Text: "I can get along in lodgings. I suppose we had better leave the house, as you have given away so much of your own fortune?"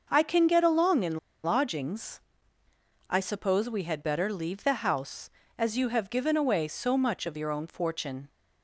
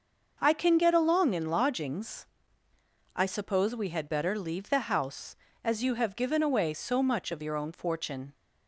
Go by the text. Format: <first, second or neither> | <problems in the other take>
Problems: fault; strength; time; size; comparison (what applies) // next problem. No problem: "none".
second | starts louder than the rest; noticeable; until 1.1 s; 6 dB; noticeable in the second // pauses between "in" and "lodgings"; slight; at 1.1 s; 0.25 s long